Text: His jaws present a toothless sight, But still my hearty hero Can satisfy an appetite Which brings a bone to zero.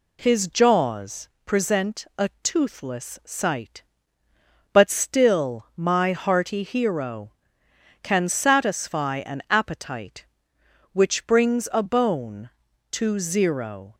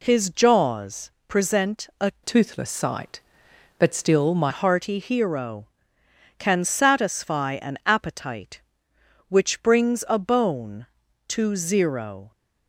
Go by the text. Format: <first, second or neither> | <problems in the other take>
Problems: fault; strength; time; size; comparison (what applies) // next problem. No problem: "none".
first | pauses between "jaws" and "present"; slight; at 1.1 s; 0.16 s long; slight in the first // changes voice from "toothless" to "my"; from 2.2 to 4.5 s; 2.3 s long